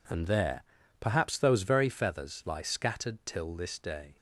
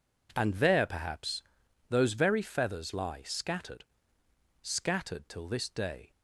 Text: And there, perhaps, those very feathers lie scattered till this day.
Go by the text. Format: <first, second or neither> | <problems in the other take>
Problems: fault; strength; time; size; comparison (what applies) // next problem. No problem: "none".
first | says "scattered" twice; at 4.6 s